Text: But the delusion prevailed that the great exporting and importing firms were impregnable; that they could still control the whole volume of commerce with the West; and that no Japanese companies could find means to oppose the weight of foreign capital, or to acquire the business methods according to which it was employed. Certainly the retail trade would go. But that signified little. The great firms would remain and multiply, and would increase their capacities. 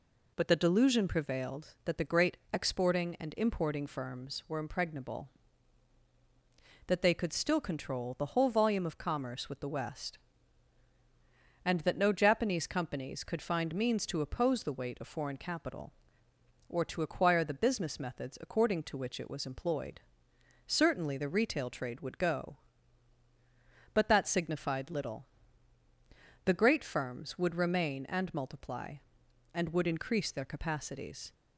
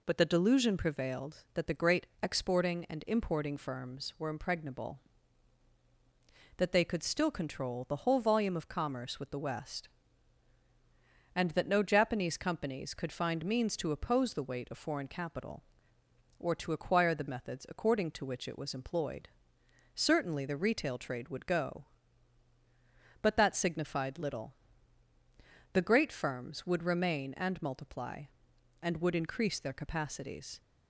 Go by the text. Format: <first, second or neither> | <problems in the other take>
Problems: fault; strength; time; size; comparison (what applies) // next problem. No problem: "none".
first | skips "business"; at 17.2 s